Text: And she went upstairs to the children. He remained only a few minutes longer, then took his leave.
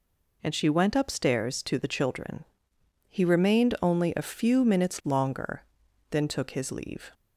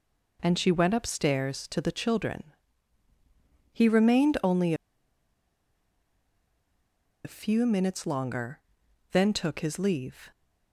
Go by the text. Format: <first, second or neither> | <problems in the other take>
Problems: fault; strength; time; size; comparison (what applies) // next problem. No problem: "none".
first | pauses between "only" and "a"; strong; at 4.7 s; 2.5 s long